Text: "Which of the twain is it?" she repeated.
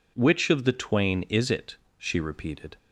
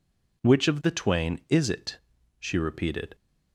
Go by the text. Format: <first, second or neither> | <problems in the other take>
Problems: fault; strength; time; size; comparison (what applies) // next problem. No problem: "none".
neither | none